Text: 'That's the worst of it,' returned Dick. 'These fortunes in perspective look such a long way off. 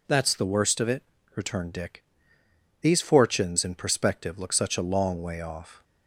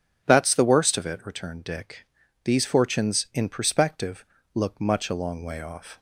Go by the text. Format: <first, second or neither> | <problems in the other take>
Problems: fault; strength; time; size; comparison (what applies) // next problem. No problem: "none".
first | starts louder than the rest; strong; until 1.2 s; 8 dB // pauses between "perspective" and "look"; slight; at 4.2 s; 0.28 s long // says "much" for "such"; at 4.7 s